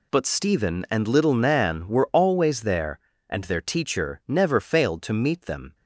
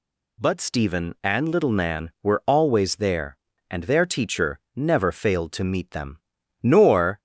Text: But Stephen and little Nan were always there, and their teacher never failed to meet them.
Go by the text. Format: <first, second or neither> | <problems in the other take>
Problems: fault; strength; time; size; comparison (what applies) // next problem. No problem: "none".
first | goes on to say "Nor"; from 6.6 s on; 0.56 s long